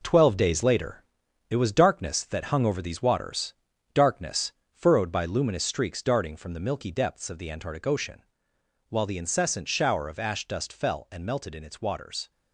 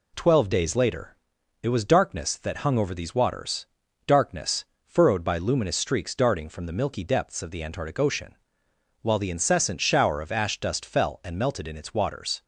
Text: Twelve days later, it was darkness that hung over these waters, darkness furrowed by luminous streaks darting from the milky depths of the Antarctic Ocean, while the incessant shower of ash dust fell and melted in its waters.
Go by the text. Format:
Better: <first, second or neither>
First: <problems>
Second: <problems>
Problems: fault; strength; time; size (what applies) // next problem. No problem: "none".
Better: second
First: gets quieter; throughout; 7 dB // pauses between "darkness" and "furrowed"; slight; at 4.5 s; 0.20 s long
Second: pauses between "darkness" and "furrowed"; slight; at 4.6 s; 0.20 s long